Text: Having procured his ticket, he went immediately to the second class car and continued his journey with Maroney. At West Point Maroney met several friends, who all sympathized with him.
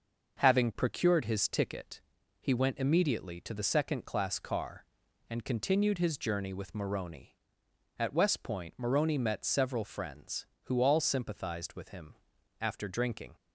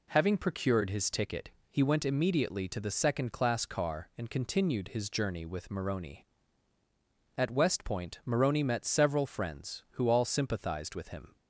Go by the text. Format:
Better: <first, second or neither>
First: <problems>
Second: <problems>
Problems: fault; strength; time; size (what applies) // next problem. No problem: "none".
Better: second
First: starts louder than the rest; noticeable; until 1.4 s; 6 dB // goes on to say "After drinking"; noticeable; from 12.5 s on; 0.76 s long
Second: none